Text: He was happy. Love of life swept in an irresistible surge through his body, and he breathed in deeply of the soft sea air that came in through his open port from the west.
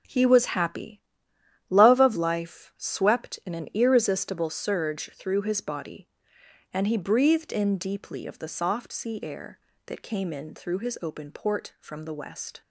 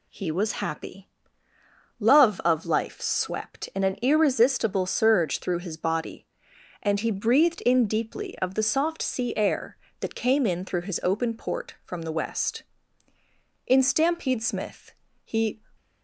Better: first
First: none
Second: goes on to say "In Stampede Smith he"; strong; from 13.6 s on; 1.9 s long

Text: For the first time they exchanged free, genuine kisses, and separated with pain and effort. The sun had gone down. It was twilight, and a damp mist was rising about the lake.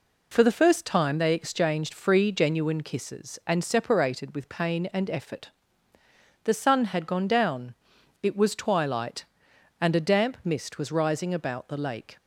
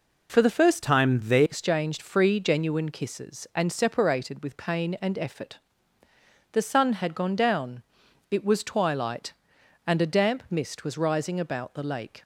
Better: first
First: none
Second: changes voice from "time" to "they"; from 0.8 to 1.4 s; 0.6 s long

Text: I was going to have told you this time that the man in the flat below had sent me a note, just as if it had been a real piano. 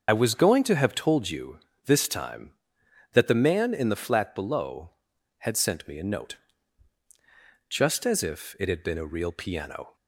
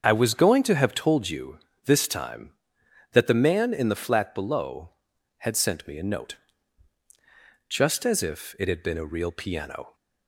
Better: second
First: loses the start of "I"; at 0.0 s; 45 ms // starts louder than the rest; until 1.1 s; 6.5 dB // pauses between "you" and "this"; slight; at 1.5 s; 0.30 s long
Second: starts louder than the rest; until 1.1 s; 7 dB // pauses between "you" and "this"; slight; at 1.5 s; 0.30 s long

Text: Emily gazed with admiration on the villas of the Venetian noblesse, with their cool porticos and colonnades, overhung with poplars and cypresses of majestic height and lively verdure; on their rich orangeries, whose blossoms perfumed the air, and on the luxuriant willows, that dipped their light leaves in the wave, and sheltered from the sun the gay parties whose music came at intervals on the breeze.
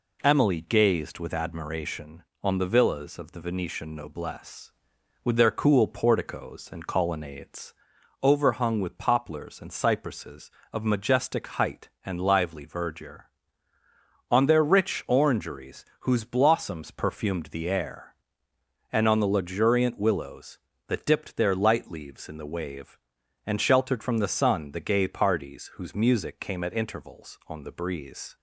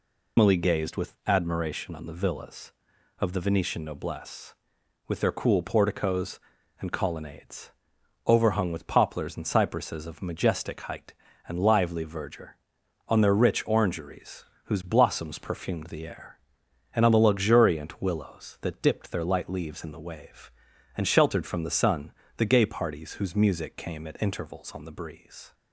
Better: first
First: none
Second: loses the start of "Emily"; at 0.3 s; 125 ms // pauses between "sun" and "the"; slight; at 22.1 s; 0.24 s long

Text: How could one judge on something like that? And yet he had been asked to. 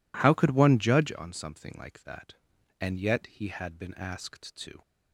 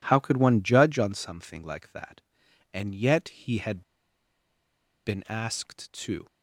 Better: first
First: none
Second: pauses between "had" and "been"; at 3.8 s; 1.2 s long

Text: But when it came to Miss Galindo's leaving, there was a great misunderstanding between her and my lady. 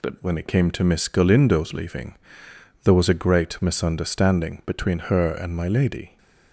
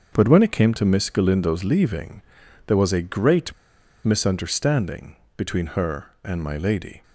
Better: first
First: none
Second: starts louder than the rest; until 1.1 s; 6.5 dB // pauses between "great" and "misunderstanding"; noticeable; at 3.5 s; 0.52 s long // pauses between "misunderstanding" and "between"; slight; at 5.1 s; 0.20 s long

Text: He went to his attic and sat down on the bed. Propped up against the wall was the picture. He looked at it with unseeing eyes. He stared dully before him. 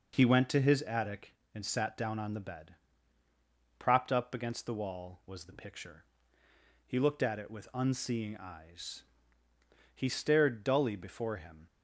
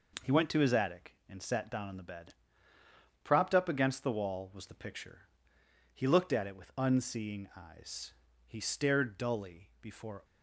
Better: first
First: none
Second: stops before "him"; at 10.2 s

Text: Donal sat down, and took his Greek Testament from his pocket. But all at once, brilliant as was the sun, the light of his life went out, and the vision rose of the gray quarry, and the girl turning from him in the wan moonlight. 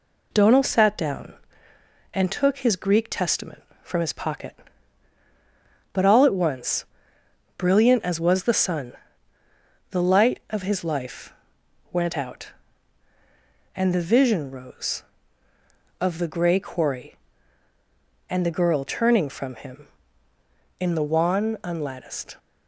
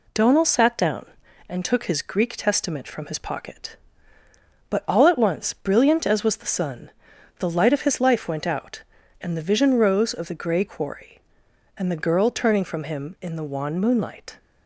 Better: second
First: pauses between "life" and "went"; noticeable; at 11.3 s; 0.58 s long // says "unlatticed" for "moonlight"; at 21.6 s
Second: none

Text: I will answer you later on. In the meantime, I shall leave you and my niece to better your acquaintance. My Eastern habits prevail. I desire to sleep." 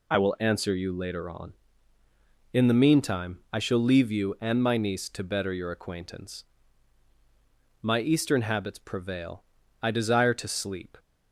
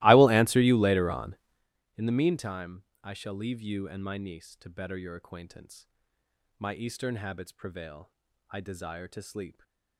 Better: first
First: none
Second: starts louder than the rest; strong; until 1.7 s; 19 dB

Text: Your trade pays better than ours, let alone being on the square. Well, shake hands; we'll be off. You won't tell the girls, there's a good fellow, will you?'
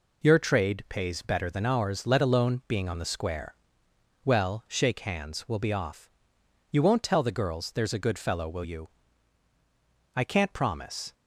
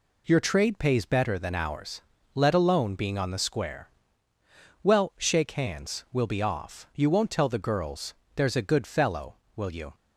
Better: second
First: goes on to say "I can't promise"; noticeable; from 10.1 s on; 0.98 s long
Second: none

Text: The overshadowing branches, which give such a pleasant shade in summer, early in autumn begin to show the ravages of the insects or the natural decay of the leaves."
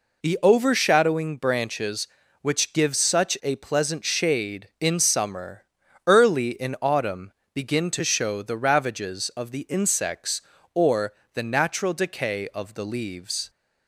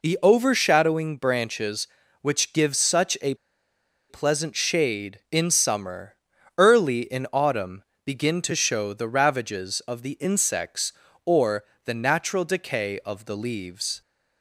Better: first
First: pauses between "autumn" and "begin"; slight; at 7.3 s; 0.22 s long // pauses between "or" and "the"; slight; at 11.1 s; 0.22 s long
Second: pauses between "a" and "pleasant"; noticeable; at 3.3 s; 0.75 s long // pauses between "autumn" and "begin"; slight; at 7.8 s; 0.22 s long // pauses between "or" and "the"; slight; at 11.6 s; 0.22 s long

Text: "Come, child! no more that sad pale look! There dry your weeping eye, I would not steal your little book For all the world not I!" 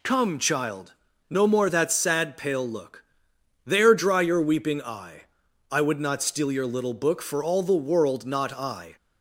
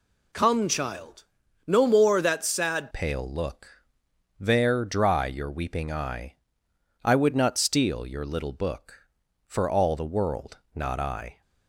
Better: first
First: none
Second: changes voice at "pale"; from 2.9 s on; 8.5 s long // pauses between "world" and "not"; slight; at 10.5 s; 0.18 s long

